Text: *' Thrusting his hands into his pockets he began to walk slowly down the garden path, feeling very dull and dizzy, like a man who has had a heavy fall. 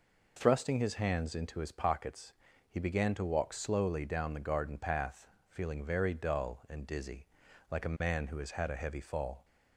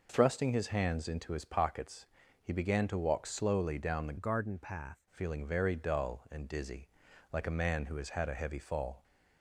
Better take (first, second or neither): first